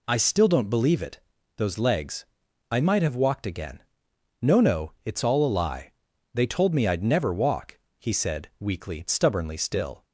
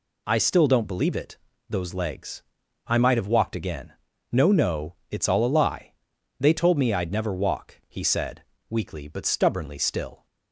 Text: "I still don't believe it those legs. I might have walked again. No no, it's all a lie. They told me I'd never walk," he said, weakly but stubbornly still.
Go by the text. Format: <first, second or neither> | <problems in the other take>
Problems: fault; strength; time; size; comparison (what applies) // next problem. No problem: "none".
second | pauses between "it" and "those"; at 1.1 s; 0.38 s long; slight in the second // skips "but"; at 9.0 s